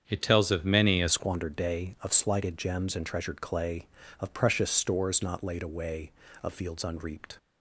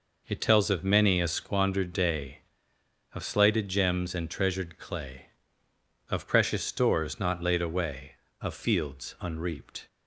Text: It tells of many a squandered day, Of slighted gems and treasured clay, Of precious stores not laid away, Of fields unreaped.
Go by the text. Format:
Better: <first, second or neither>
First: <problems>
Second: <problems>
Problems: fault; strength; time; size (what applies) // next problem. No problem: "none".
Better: second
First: starts louder than the rest; strong; until 1.0 s; 7.5 dB // changes voice at "squandered"; from 1.0 s on; 6.3 s long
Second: none